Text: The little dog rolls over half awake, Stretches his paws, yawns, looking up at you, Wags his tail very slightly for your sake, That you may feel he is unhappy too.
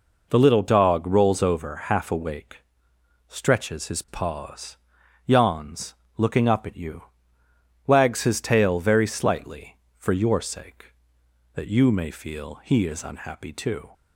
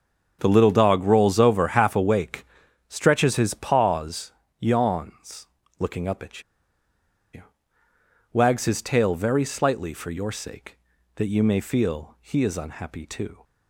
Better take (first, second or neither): first